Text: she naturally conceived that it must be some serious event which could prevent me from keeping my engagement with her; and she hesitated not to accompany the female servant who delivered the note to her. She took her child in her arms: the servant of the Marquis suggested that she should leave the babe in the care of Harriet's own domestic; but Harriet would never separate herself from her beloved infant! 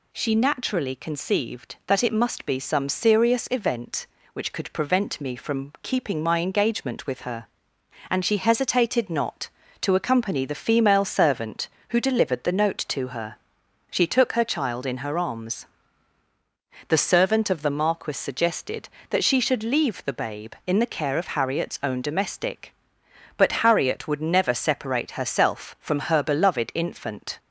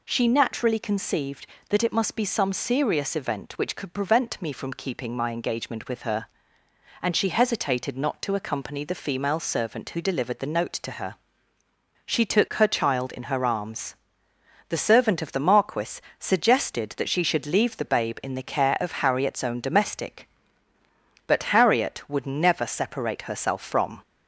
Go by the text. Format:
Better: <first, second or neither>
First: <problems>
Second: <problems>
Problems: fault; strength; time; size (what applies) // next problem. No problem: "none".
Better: first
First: none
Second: pauses between "Marquis" and "suggested"; slight; at 15.9 s; 0.20 s long // stops before "her beloved infant"; at 24.0 s